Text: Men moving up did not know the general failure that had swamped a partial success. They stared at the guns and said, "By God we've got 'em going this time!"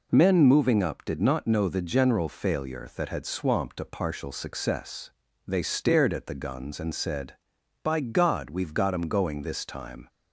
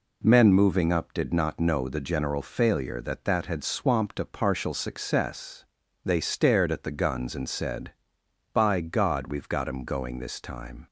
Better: first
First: none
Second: says "that" twice; at 3.2 s

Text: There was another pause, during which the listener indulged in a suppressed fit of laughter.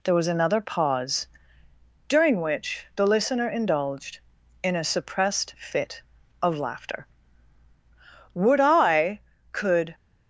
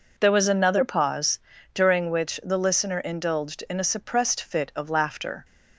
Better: second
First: goes on to say "Would I could"; from 8.3 s on; 1.6 s long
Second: none

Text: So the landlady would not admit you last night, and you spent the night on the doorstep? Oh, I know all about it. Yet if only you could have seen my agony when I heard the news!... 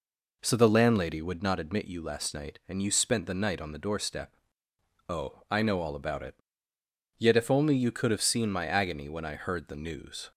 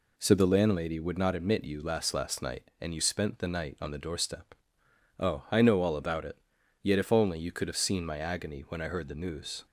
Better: first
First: none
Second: says "last" twice; at 2.1 s

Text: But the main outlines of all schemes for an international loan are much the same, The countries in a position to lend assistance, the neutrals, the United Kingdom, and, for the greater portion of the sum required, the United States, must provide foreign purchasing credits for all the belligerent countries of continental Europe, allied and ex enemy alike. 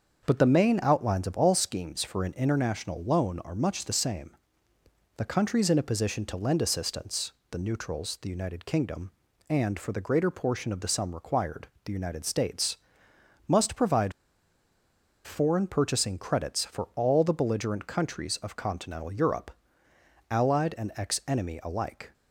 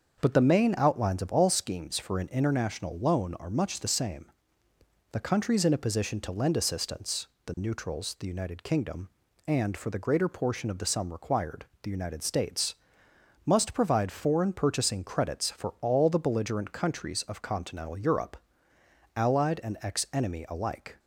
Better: second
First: starts louder than the rest; until 1.2 s; 6.5 dB // pauses between "provide" and "foreign"; at 14.1 s; 1.1 s long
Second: starts louder than the rest; until 1.2 s; 6.5 dB

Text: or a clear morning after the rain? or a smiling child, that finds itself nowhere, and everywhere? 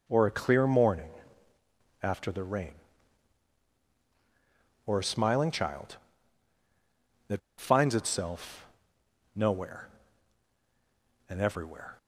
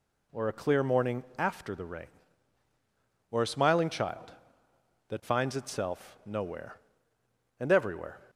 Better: second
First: pauses between "morning" and "after"; noticeable; at 1.1 s; 0.92 s long // pauses between "that" and "finds"; slight; at 7.4 s; 0.18 s long // pauses between "itself" and "nowhere"; noticeable; at 8.6 s; 0.66 s long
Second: none

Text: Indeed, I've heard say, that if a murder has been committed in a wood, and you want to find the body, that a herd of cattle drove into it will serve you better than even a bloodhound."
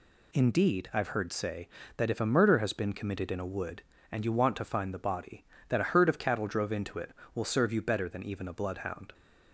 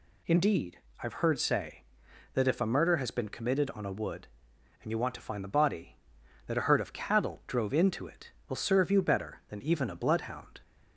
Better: first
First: none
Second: says "on" for "in"; at 3.7 s

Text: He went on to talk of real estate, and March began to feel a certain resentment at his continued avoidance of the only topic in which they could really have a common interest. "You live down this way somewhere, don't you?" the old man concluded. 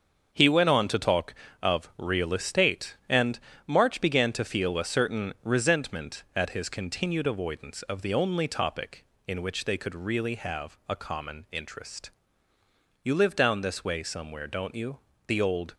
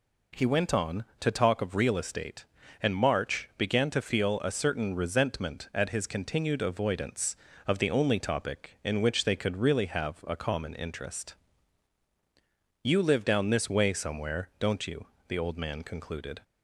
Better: second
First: starts louder than the rest; until 1.3 s; 6.5 dB // pauses between "and" and "March"; slight; at 3.3 s; 0.28 s long // stops before "man concluded"; at 15.7 s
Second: none

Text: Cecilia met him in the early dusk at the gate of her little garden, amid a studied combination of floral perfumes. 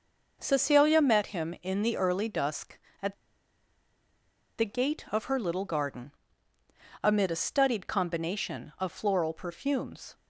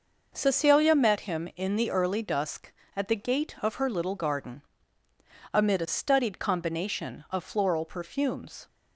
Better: second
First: pauses between "at" and "the"; strong; at 3.1 s; 1.4 s long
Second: none

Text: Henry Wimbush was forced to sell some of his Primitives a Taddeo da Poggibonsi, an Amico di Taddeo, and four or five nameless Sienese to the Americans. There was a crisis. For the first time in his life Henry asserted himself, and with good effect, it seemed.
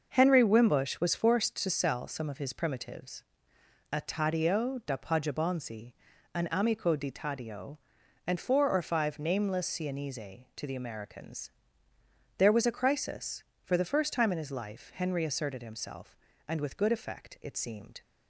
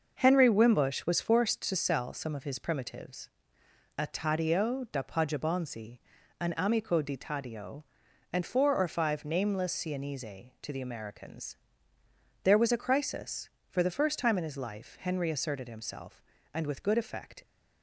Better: first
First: pauses between "Primitives" and "a"; noticeable; at 3.2 s; 0.70 s long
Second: pauses between "Primitives" and "a"; noticeable; at 3.2 s; 0.70 s long // stops before "it seemed"; at 17.4 s

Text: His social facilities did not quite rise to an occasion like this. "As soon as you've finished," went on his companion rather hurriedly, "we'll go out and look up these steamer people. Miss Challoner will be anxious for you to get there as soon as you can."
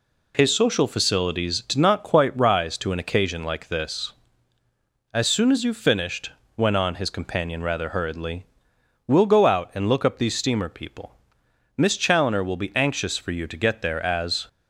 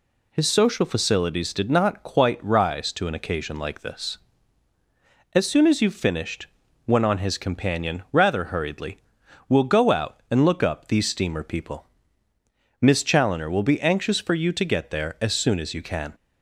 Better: second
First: stops before "soon as you can"; at 14.4 s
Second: none

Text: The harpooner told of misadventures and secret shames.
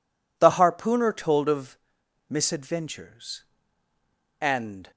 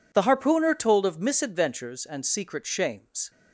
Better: second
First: pauses between "of" and "misadventures"; noticeable; at 1.7 s; 0.50 s long // stops before "secret shames"; at 4.9 s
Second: none

